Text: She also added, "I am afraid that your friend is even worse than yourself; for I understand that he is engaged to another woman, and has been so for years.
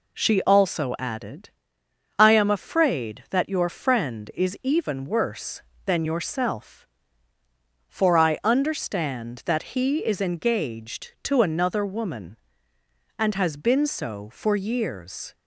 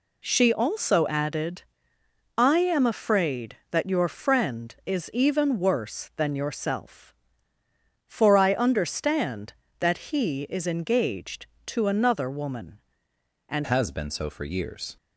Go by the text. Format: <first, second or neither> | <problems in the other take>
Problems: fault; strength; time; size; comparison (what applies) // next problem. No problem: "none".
first | changes voice at "has"; from 13.6 s on; 1.3 s long